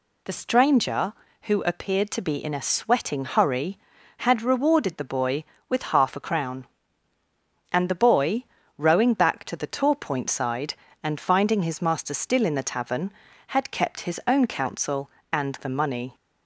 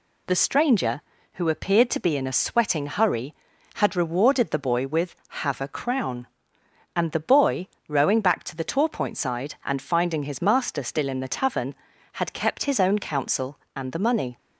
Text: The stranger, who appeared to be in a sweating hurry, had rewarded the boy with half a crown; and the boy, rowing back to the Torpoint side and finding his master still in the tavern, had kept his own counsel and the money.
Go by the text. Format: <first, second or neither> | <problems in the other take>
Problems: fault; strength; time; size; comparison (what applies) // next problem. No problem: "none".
first | says "have" for "half"; at 5.2 s